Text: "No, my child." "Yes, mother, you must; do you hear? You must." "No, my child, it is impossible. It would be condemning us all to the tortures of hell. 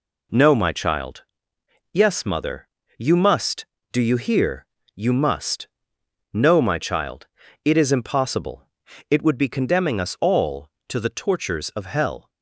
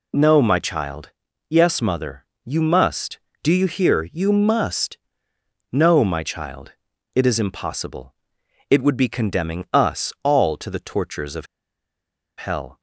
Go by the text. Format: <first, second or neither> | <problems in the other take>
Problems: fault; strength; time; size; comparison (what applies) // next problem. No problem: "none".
first | pauses between "of" and "hell"; noticeable; at 11.4 s; 0.92 s long